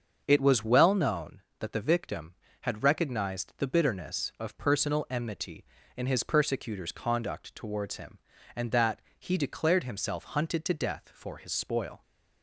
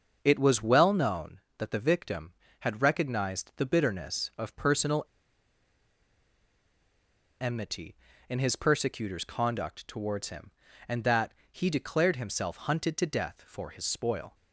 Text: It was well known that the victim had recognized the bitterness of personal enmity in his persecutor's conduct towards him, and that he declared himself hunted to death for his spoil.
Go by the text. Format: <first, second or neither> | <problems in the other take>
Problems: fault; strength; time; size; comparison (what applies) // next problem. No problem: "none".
first | starts louder than the rest; until 1.2 s; 6.5 dB; also in the first // pauses between "personal" and "enmity"; strong; at 5.0 s; 2.3 s long // pauses between "that" and "he"; slight; at 11.3 s; 0.18 s long; slight in the first